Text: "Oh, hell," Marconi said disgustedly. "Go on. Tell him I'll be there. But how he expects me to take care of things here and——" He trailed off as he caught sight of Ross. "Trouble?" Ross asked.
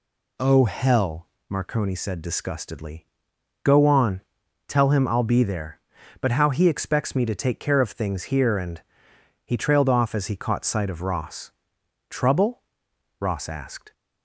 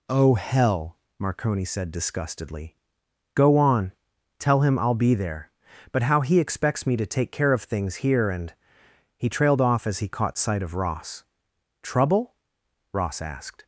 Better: neither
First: none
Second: none

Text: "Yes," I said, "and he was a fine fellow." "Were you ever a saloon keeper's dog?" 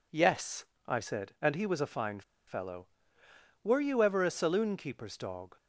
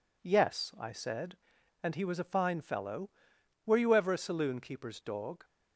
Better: second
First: pauses between "fine" and "fellow"; slight; at 2.2 s; 0.26 s long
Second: none

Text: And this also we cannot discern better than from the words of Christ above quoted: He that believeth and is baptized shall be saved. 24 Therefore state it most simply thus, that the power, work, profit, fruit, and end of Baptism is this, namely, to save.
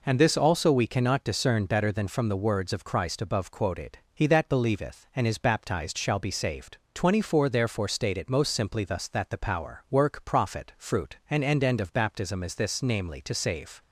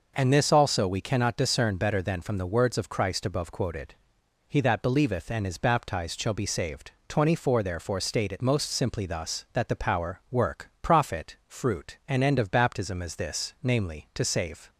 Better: second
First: says "end" twice; at 11.6 s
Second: none

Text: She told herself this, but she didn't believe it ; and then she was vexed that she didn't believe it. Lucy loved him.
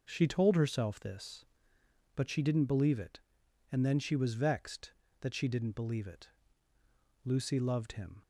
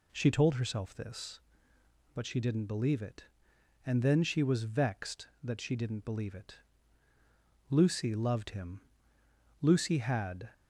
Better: first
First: none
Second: goes on to say "Lucy had"; noticeable; from 9.6 s on; 0.90 s long

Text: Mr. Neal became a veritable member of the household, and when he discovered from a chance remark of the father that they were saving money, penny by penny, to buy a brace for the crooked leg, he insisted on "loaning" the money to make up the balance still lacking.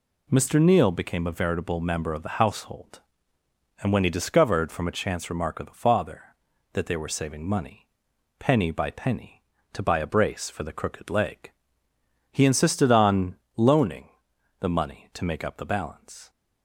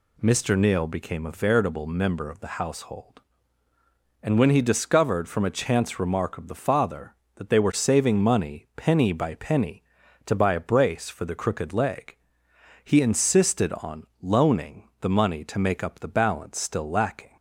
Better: second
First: pauses between "on" and "loaning"; slight; at 13.3 s; 0.20 s long // pauses between "loaning" and "the"; noticeable; at 14.0 s; 0.50 s long // stops before "still lacking"; at 16.2 s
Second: pauses between "on" and "loaning"; slight; at 14.0 s; 0.16 s long

